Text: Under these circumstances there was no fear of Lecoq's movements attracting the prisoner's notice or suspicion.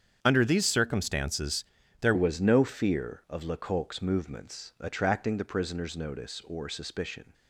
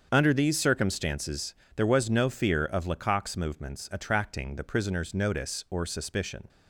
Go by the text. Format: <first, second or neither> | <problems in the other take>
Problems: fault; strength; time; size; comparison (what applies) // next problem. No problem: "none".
second | starts louder than the rest; strong; until 1.2 s; 8 dB; also in the second // pauses between "circumstances" and "there"; at 1.6 s; 0.38 s long; slight in the second // changes voice at "was"; from 2.1 s on; 5.2 s long